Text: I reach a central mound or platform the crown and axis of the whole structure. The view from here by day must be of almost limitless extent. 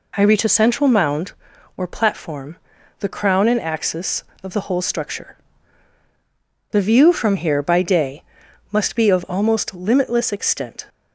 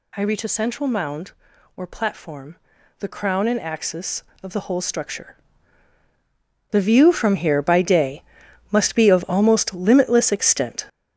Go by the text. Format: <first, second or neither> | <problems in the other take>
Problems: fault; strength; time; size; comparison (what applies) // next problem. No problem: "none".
first | gets louder; strong; throughout; 7.5 dB // pauses between "platform" and "the"; at 2.5 s; 0.44 s long; also in the first // pauses between "day" and "must"; noticeable; at 8.2 s; 0.48 s long; noticeable in the first